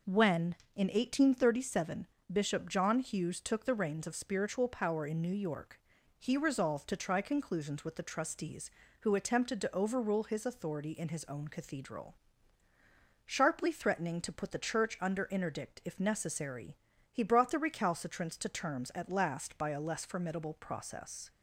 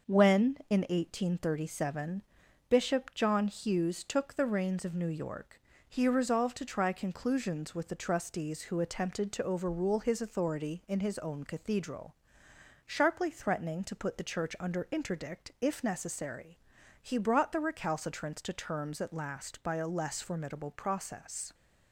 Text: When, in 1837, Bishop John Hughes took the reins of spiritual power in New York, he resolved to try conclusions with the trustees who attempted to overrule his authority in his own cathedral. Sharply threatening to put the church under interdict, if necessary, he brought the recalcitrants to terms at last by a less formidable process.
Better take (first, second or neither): first